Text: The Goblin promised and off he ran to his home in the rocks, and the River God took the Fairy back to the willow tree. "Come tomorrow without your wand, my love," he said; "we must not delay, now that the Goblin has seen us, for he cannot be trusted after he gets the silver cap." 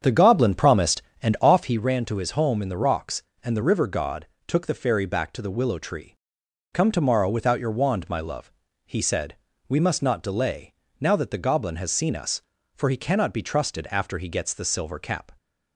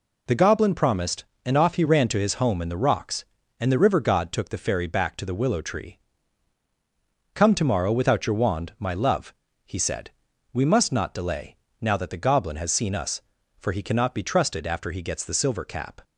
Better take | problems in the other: second | starts louder than the rest; strong; until 1.8 s; 7.5 dB // pauses between "God" and "took"; slight; at 4.2 s; 0.22 s long

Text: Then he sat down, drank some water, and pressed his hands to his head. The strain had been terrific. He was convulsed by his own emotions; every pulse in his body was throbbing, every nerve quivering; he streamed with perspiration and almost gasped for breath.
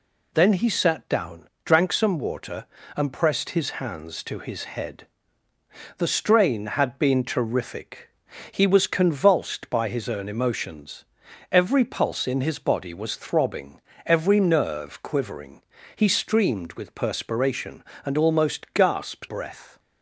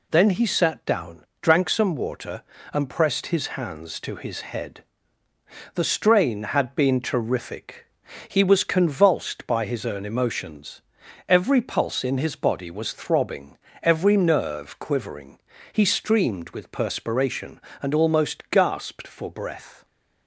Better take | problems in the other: second | skips "for"; at 19.2 s

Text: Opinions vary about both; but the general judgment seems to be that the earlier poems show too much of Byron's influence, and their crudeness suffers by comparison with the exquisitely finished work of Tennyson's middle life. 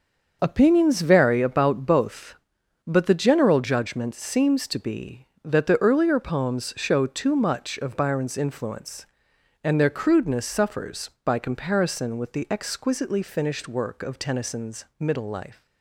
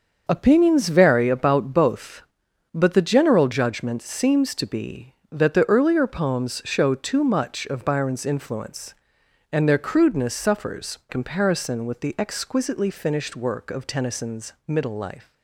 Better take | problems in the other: first | starts louder than the rest; until 1.3 s; 6 dB; also in the first // skips "by"; at 11.0 s

